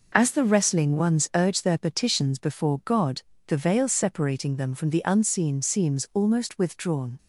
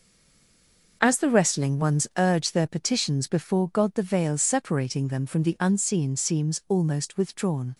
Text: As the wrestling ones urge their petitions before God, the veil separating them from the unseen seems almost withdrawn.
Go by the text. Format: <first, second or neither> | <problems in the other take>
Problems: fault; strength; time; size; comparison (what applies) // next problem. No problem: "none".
first | stays silent before the first word; until 1.0 s; 1.0 s long